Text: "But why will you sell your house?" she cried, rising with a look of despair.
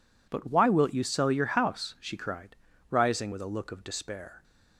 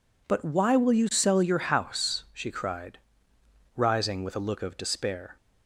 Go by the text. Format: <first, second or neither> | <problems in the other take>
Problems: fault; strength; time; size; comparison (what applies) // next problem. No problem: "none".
second | says "wilt" for "will"; at 0.6 s